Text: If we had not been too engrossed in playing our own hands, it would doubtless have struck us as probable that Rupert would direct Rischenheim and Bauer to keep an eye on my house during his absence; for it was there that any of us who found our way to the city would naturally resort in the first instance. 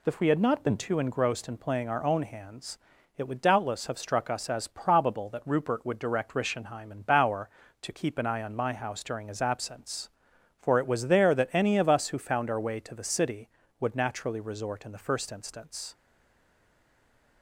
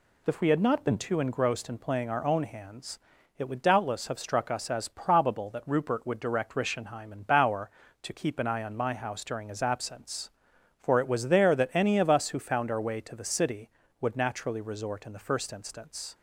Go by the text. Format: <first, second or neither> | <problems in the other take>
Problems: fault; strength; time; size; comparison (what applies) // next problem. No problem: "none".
second | stays silent after the last word; noticeable; from 15.9 s on; 1.5 s long